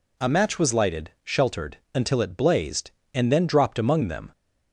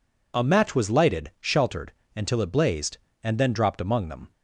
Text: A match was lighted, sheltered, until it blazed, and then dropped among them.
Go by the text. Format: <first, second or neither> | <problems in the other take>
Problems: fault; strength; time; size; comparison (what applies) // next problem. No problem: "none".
neither | none